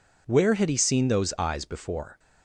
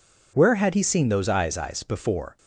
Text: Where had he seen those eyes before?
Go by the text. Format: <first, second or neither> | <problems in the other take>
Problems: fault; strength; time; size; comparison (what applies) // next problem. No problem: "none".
first | says "eyes" twice; at 1.5 s